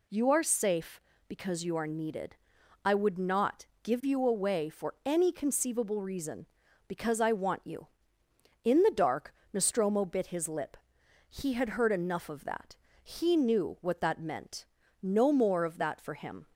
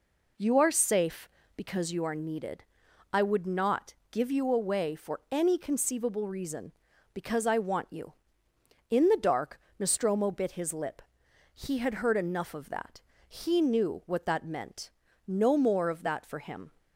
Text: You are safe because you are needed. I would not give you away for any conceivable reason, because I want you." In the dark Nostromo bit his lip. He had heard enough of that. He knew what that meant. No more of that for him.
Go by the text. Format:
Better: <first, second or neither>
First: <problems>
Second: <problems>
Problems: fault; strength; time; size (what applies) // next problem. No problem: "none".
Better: first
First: pauses between "not" and "give"; slight; at 3.6 s; 0.18 s long // pauses between "dark" and "Nostromo"; slight; at 9.3 s; 0.18 s long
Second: starts louder than the rest; until 2.1 s; 3.5 dB // pauses between "not" and "give"; slight; at 3.9 s; 0.18 s long // pauses between "dark" and "Nostromo"; slight; at 9.5 s; 0.18 s long